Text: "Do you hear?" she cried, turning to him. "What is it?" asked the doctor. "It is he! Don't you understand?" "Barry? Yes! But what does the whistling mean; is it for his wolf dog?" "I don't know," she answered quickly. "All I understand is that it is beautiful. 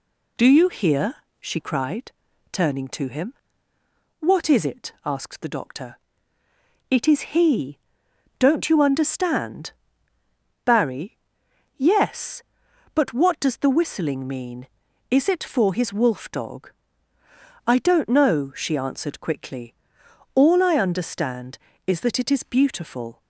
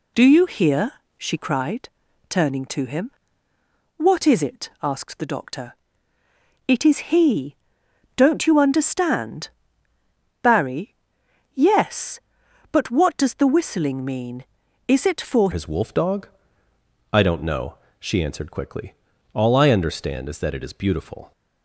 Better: first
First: none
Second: changes voice at "his"; from 15.5 s on; 5.8 s long

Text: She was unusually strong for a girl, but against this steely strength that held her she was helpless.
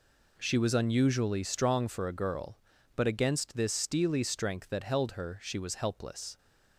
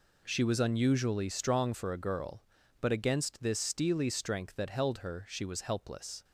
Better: neither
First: none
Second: none

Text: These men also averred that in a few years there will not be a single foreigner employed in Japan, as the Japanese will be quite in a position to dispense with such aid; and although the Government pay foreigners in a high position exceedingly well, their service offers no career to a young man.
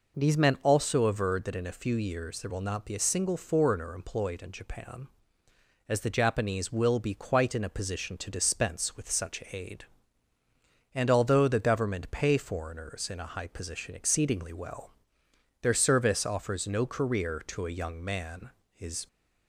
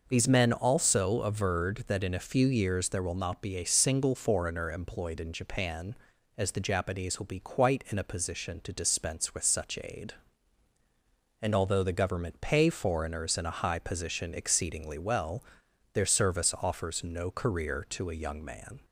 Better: second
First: goes on to say "His"; slight; from 18.7 s on; 0.36 s long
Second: none

